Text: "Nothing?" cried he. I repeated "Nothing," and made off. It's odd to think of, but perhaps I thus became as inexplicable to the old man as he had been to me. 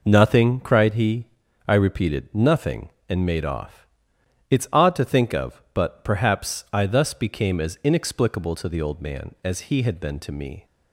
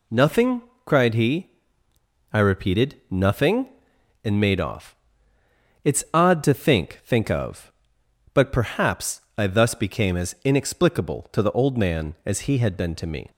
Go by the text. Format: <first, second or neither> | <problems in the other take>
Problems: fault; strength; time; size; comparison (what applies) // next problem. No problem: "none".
first | says "think" twice; at 7.0 s // pauses between "perhaps" and "I"; slight; at 9.2 s; 0.16 s long